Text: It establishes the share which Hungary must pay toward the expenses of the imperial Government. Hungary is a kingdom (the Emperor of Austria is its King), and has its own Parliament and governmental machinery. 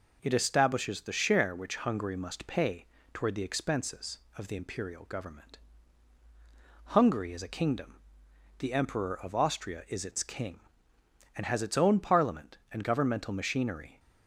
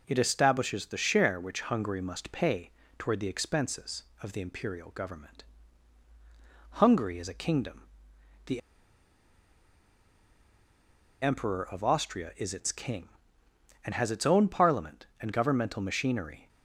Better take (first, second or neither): first